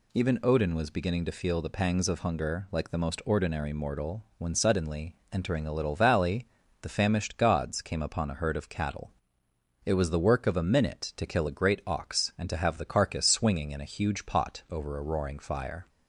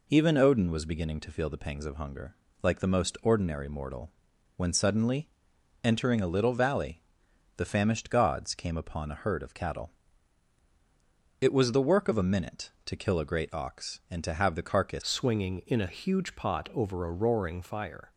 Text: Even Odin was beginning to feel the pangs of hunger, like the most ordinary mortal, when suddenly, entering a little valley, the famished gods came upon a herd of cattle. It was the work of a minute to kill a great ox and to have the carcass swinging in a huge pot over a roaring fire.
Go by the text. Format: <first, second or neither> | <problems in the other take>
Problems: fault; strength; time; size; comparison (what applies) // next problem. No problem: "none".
first | changes voice at "swinging"; from 15.0 s on; 3.1 s long